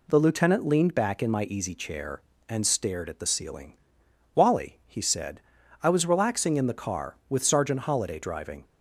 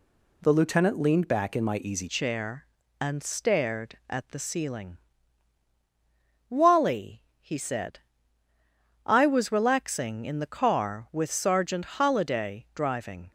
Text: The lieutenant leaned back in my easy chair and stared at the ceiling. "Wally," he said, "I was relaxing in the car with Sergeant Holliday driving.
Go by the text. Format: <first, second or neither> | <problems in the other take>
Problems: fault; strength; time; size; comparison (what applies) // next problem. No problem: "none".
first | changes voice at "chair"; from 2.0 s on; 11.3 s long